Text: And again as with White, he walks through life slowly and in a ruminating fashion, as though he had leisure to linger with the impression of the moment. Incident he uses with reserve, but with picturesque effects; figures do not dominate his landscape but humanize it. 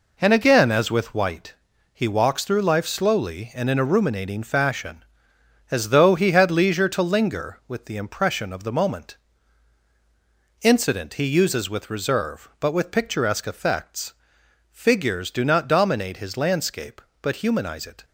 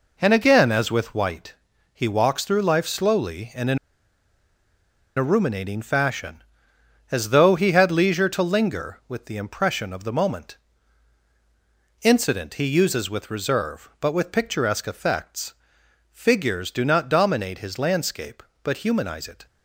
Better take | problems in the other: first | pauses between "in" and "a"; strong; at 3.7 s; 1.3 s long

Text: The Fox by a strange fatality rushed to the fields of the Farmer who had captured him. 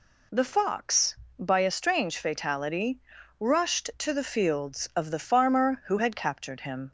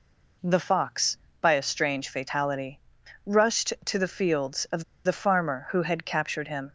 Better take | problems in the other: first | pauses between "fatality" and "rushed"; noticeable; at 2.7 s; 0.46 s long; also in the first // pauses between "of" and "the"; slight; at 4.8 s; 0.22 s long

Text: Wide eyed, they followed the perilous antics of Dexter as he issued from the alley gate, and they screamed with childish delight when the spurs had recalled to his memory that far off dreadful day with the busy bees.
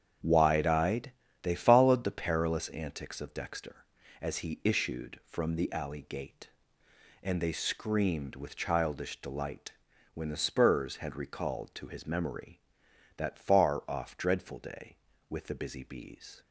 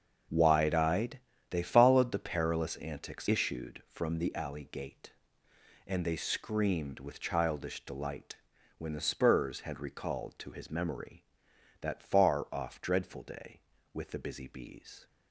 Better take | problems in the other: first | starts louder than the rest; until 1.5 s; 6.5 dB; strong in the first // skips "of Dexter as he"; at 3.2 s // pauses between "delight" and "when"; at 8.3 s; 0.40 s long; also in the first

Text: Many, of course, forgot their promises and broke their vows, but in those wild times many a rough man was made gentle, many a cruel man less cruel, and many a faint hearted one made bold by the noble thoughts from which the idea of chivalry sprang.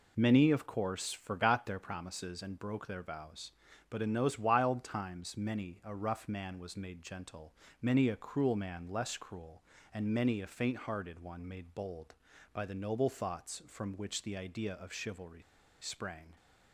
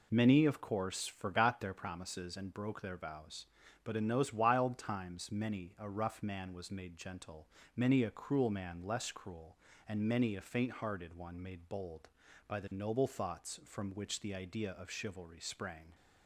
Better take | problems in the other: second | pauses between "chivalry" and "sprang"; at 15.4 s; 0.40 s long

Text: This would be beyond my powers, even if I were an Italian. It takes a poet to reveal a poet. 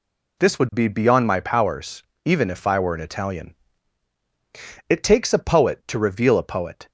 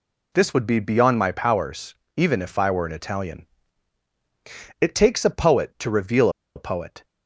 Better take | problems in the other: first | pauses between "reveal" and "a"; slight; at 6.3 s; 0.25 s long

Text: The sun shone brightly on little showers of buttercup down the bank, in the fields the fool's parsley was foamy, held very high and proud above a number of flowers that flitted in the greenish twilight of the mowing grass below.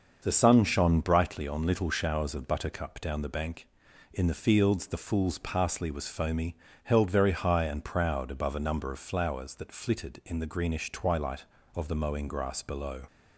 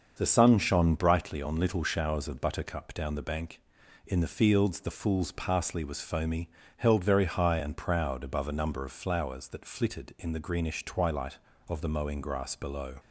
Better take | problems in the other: neither | starts louder than the rest; the same in both

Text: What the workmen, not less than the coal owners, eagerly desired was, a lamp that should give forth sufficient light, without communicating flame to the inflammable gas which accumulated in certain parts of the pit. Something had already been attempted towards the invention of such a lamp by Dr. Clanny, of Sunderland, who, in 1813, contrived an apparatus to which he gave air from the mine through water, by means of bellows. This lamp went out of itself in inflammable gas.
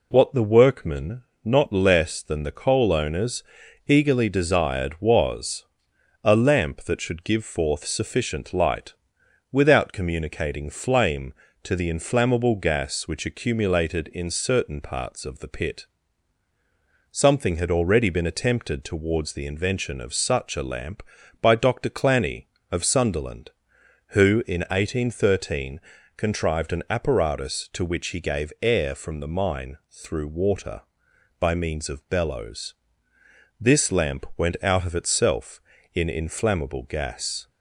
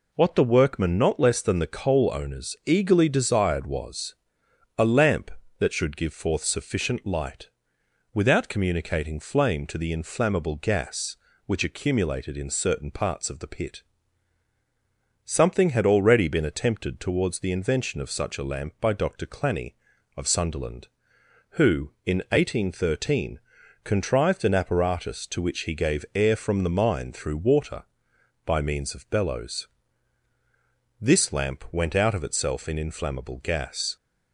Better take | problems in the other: neither | none

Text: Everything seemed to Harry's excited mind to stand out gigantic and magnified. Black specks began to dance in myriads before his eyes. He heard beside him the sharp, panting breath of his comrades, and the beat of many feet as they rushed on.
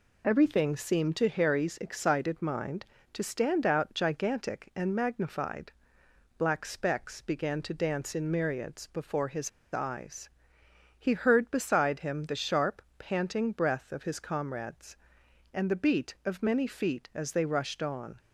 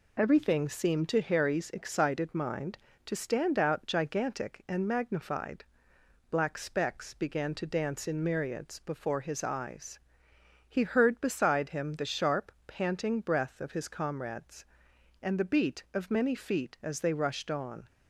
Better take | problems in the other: second | pauses between "his" and "eyes"; slight; at 9.4 s; 0.24 s long

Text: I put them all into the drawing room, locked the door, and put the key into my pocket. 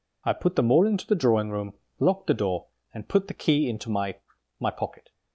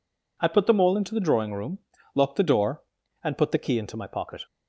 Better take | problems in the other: second | says "my" twice; at 4.5 s

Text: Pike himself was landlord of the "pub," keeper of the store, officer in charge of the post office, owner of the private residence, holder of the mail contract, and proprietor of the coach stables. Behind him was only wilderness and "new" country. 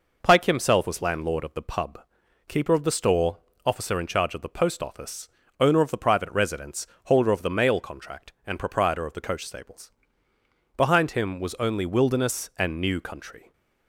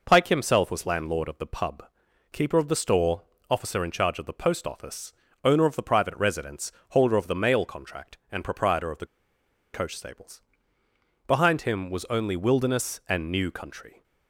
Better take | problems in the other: first | pauses between "the" and "coach"; noticeable; at 9.0 s; 0.66 s long

